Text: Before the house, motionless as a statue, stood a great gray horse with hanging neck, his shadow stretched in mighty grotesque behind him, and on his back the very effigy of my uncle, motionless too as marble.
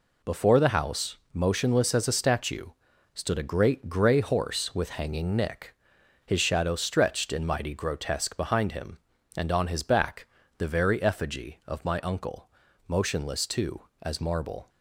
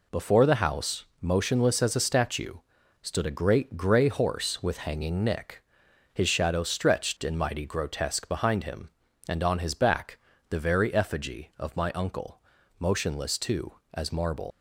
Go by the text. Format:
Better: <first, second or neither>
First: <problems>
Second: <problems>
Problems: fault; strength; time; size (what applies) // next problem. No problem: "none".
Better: first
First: pauses between "back" and "the"; slight; at 10.2 s; 0.30 s long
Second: pauses between "back" and "the"; slight; at 10.1 s; 0.30 s long // leaves "marble" unfinished; at 14.5 s; 100 ms